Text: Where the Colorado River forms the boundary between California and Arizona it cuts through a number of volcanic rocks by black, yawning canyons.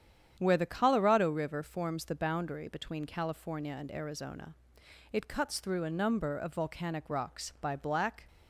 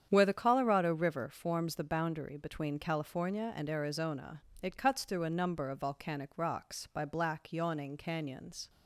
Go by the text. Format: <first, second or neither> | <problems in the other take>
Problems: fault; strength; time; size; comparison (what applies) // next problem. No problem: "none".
second | starts louder than the rest; strong; until 1.3 s; 9 dB; strong in the second // pauses between "Arizona" and "it"; noticeable; at 4.5 s; 0.60 s long; slight in the second // stops before "yawning canyons"; at 8.2 s